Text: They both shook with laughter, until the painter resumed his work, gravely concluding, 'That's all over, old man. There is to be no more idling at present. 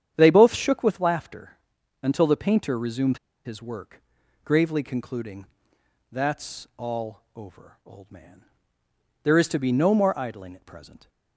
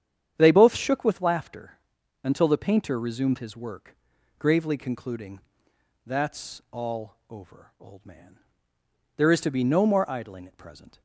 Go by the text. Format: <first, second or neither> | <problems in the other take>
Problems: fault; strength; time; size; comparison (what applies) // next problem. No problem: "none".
second | starts louder than the rest; strong; until 1.1 s; 9 dB; strong in the second // pauses between "resumed" and "his"; slight; at 3.1 s; 0.27 s long